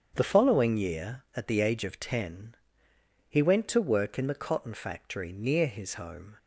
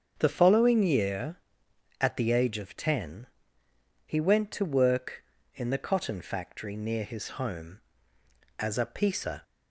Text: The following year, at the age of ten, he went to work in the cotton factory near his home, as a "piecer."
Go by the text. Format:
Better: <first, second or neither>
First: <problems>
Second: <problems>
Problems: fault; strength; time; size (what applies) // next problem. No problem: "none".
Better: second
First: starts louder than the rest; strong; until 1.1 s; 8 dB // stops before "as a piecer"; at 6.3 s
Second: starts louder than the rest; until 1.2 s; 7 dB